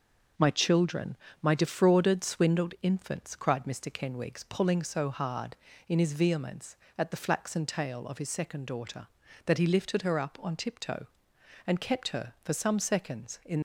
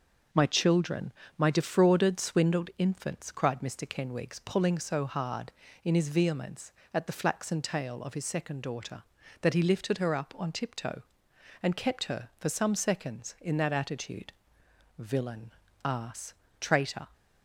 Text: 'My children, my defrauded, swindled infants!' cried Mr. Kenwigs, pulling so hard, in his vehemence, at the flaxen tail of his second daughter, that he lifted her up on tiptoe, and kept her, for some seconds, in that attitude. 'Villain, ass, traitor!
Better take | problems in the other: second | starts louder than the rest; noticeable; until 1.6 s; 6 dB; noticeable in the second // stops before "that attitude Villain ass traitor"; at 13.5 s

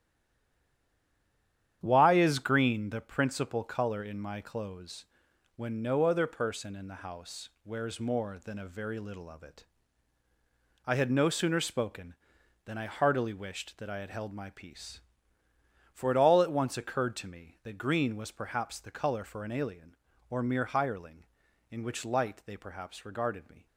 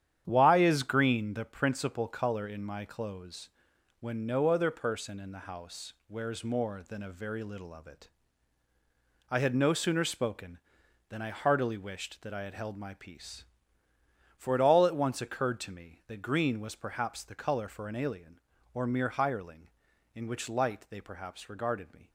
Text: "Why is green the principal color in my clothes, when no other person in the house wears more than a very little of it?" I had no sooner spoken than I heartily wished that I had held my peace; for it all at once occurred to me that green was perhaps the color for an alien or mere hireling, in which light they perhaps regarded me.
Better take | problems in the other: second | stays silent before the first word; noticeable; until 1.8 s; 1.8 s long // starts louder than the rest; strong; until 2.8 s; 9.5 dB; strong in the second // pauses between "house" and "wears"; slight; at 7.4 s; 0.16 s long; slight in the second

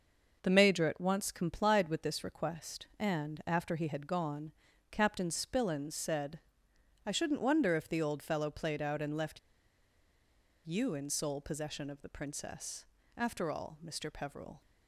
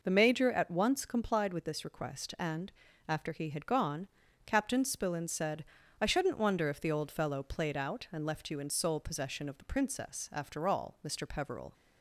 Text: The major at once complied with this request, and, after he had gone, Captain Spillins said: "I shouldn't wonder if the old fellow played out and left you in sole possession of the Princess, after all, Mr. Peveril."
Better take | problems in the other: second | pauses between "left" and "you"; strong; at 9.3 s; 1.2 s long

